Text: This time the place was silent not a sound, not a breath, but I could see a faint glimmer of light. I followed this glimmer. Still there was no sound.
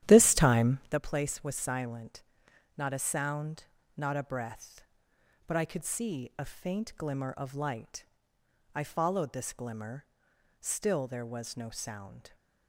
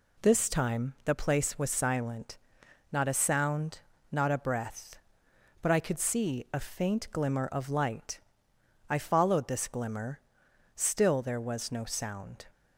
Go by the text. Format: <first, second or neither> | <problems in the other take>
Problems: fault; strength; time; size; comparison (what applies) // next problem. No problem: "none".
second | starts louder than the rest; strong; until 1.0 s; 11.5 dB // pauses between "silent" and "not"; noticeable; at 2.2 s; 0.54 s long; noticeable in the second